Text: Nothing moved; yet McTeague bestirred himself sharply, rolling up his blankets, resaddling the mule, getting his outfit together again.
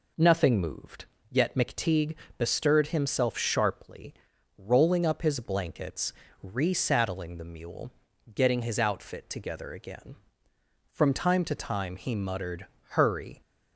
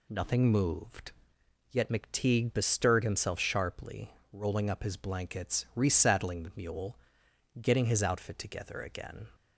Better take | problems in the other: second | pauses between "McTeague" and "bestirred"; slight; at 2.1 s; 0.24 s long // goes on to say "From time to time he muttered Hurry"; strong; from 10.9 s on; 2.4 s long

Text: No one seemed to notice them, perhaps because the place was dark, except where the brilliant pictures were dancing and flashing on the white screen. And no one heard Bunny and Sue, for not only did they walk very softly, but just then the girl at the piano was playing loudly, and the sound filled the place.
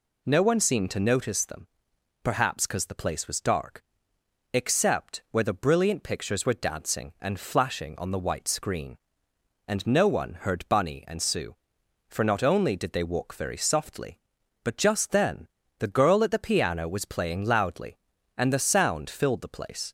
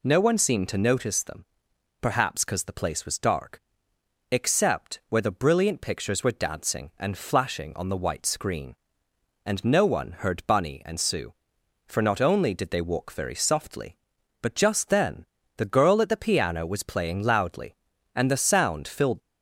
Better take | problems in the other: first | pauses between "then" and "the"; slight; at 15.2 s; 0.32 s long; slight in the first // stops before "the place"; at 19.1 s

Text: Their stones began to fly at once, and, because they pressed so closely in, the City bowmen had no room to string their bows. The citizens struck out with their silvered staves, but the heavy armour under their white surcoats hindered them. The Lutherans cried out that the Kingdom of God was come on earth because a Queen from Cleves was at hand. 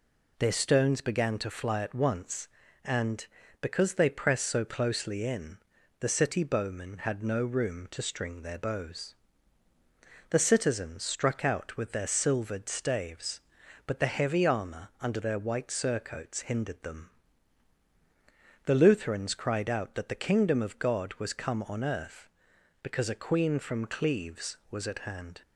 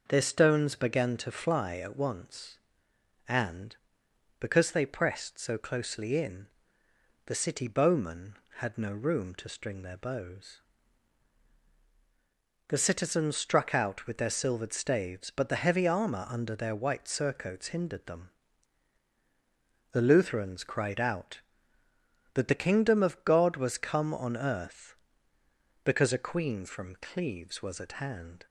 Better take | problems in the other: neither | none

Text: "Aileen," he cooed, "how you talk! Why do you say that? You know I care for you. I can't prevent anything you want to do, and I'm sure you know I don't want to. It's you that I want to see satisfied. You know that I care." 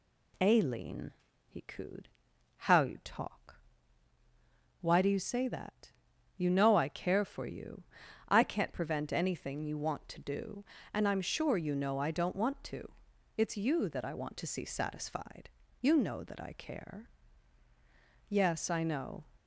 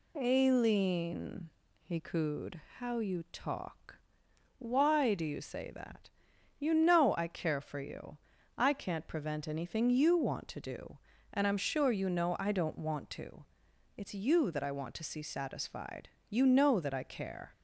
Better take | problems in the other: second | goes on to say "Yes I know"; noticeable; from 18.2 s on; 0.96 s long

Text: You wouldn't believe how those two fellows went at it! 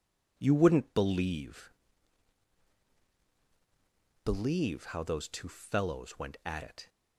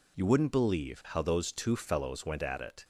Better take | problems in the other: second | says "believe" twice; at 4.2 s

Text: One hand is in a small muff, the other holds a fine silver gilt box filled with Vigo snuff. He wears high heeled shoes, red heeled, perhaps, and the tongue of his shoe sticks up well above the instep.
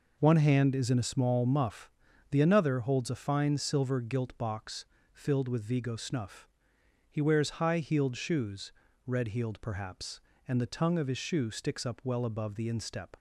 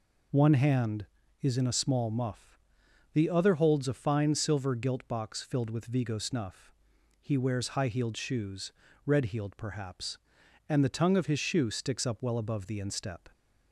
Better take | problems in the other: second | says "another" for "other"; at 2.3 s // pauses between "box" and "filled"; slight; at 4.8 s; 0.30 s long

